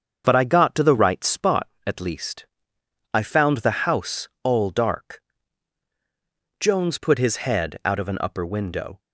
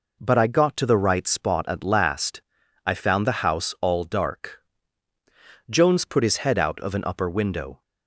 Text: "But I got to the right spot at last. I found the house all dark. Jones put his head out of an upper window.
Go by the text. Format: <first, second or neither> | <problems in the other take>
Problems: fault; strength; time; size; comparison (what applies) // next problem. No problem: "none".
second | starts louder than the rest; until 1.2 s; 7 dB // says "least" for "last"; at 2.0 s // pauses between "house" and "all"; slight; at 4.2 s; 0.16 s long